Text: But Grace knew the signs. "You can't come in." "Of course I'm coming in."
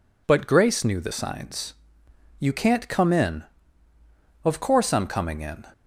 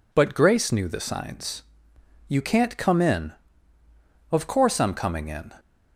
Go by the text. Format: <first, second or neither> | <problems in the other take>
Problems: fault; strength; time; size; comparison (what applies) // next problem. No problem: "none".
neither | none